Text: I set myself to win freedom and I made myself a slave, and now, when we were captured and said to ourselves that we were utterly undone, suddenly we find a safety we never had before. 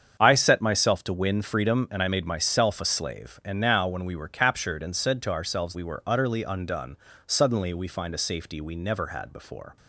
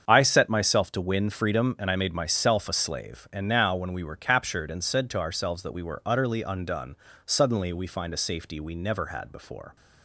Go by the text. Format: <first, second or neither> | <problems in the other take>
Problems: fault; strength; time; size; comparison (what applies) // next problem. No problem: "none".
second | starts louder than the rest; strong; until 1.2 s; 7.5 dB; strong in the second // skips "that"; at 5.7 s